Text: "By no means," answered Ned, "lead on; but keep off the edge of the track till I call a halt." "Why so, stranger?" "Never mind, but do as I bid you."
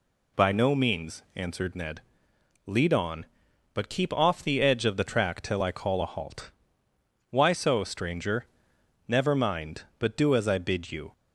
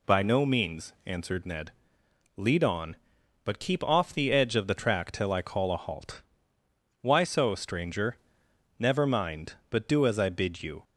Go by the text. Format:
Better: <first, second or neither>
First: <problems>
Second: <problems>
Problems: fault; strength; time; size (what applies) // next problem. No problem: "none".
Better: neither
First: none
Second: none